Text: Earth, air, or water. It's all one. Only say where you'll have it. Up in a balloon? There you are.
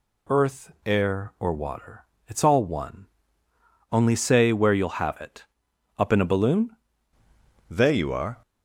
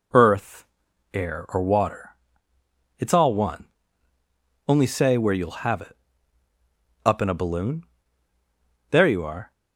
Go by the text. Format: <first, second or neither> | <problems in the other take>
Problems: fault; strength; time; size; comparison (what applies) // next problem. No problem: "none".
second | changes voice at "There"; from 7.6 s on; 0.8 s long